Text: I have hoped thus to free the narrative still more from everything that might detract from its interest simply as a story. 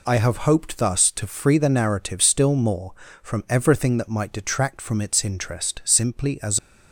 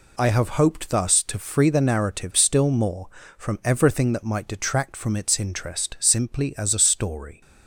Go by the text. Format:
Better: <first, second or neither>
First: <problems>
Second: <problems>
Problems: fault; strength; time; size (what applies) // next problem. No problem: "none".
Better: second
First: stops before "a story"; at 6.5 s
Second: none